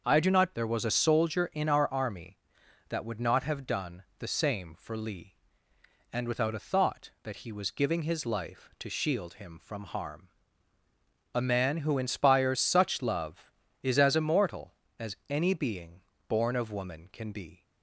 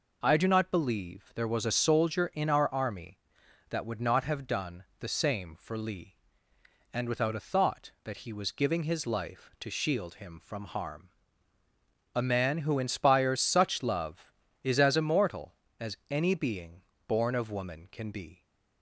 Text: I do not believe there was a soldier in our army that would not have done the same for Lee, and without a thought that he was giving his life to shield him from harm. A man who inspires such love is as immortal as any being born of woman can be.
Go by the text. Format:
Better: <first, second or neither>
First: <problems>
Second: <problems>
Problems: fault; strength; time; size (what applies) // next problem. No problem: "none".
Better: second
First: starts louder than the rest; until 1.0 s; 6.5 dB // skips "believe"; at 0.5 s // pauses between "done" and "the"; slight; at 4.0 s; 0.16 s long // pauses between "being" and "born"; slight; at 16.0 s; 0.28 s long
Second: pauses between "done" and "the"; slight; at 4.8 s; 0.16 s long // pauses between "being" and "born"; slight; at 16.8 s; 0.26 s long